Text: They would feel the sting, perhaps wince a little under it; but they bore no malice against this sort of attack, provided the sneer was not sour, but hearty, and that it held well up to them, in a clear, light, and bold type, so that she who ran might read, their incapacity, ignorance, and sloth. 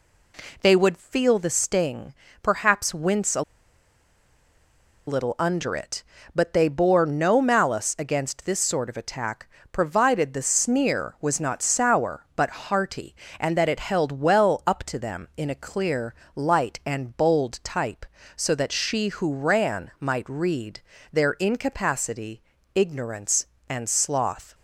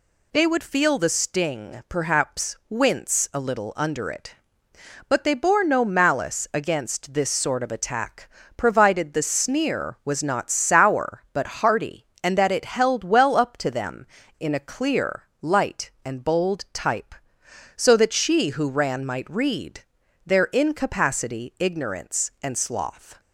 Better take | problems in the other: second | pauses between "a" and "little"; strong; at 3.4 s; 1.6 s long

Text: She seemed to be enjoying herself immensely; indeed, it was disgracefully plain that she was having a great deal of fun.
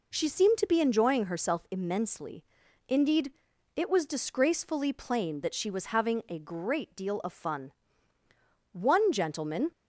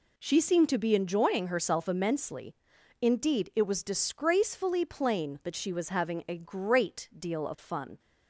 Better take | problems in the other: second | goes on to say "One gentleman"; noticeable; from 8.7 s on; 0.98 s long

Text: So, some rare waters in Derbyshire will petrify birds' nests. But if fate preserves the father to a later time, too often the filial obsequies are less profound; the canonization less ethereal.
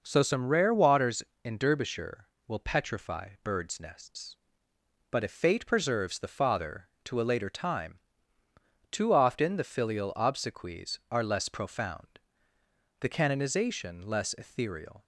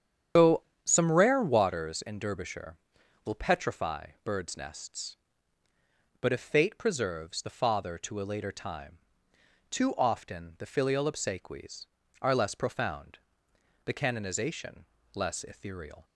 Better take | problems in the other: first | loses the start of "So"; at 0.3 s; 80 ms // starts louder than the rest; strong; until 1.6 s; 8.5 dB // pauses between "petrify" and "birds"; slight; at 4.0 s; 0.16 s long // pauses between "canonization" and "less"; slight; at 14.8 s; 0.30 s long

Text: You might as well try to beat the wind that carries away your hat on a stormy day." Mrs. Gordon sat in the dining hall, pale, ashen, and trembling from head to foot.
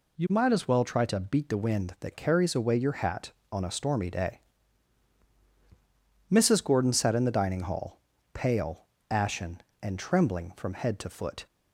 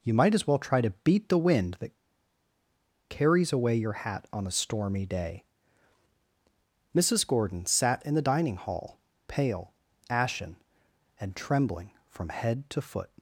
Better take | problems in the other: first | pauses between "that" and "carries"; at 1.9 s; 1.1 s long

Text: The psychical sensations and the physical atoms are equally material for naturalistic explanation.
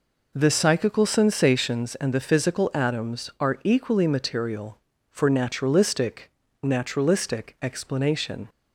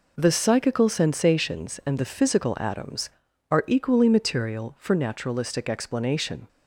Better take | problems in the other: second | says "naturalistic" twice; at 6.6 s

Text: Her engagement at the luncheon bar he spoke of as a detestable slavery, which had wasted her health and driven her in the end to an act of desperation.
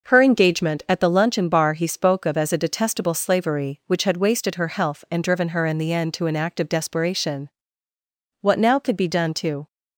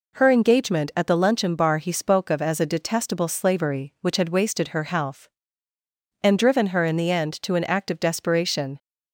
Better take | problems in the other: second | goes on to say "What now could be done to"; noticeable; from 8.4 s on; 1.2 s long

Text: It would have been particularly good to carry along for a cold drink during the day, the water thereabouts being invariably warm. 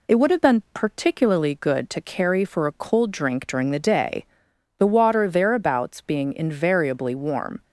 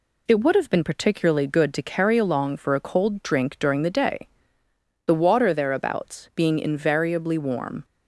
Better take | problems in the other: second | skips "along"; at 2.4 s

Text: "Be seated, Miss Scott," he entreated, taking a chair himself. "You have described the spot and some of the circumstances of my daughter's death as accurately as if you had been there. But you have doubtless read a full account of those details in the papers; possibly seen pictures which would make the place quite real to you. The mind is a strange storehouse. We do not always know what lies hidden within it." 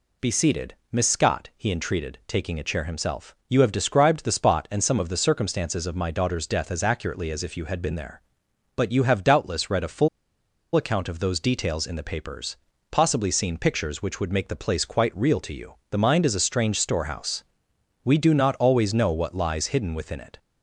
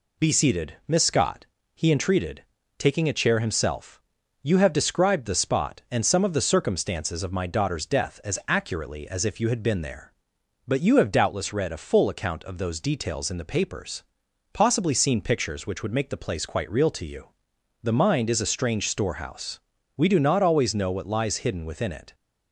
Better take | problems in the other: second | pauses between "full" and "account"; noticeable; at 10.0 s; 0.67 s long

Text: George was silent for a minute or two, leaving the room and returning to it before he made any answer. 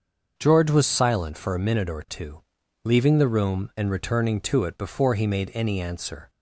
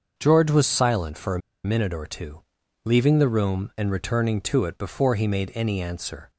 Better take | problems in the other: first | starts louder than the rest; until 1.1 s; 6.5 dB; also in the first // pauses between "a" and "minute"; slight; at 1.4 s; 0.24 s long

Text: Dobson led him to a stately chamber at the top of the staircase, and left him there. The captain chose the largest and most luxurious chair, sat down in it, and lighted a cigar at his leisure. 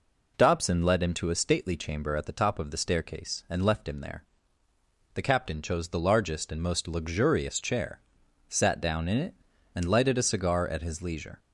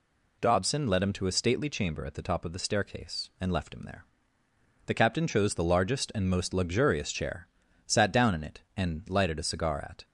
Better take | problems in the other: first | stops before "his leisure"; at 10.0 s

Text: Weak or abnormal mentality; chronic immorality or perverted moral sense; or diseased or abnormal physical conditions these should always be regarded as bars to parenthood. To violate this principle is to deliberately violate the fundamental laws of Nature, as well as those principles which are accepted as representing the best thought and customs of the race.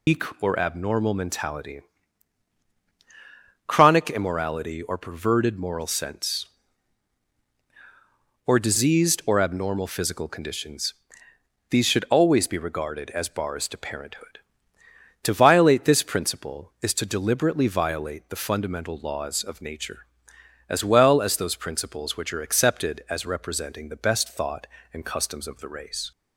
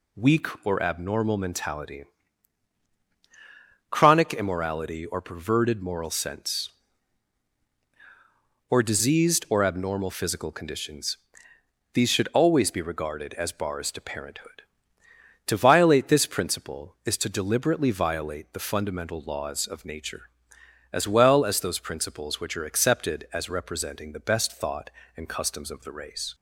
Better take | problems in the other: second | loses the start of "Weak"; at 0.0 s; 140 ms // pauses between "conditions" and "these"; noticeable; at 10.9 s; 0.76 s long; noticeable in the second

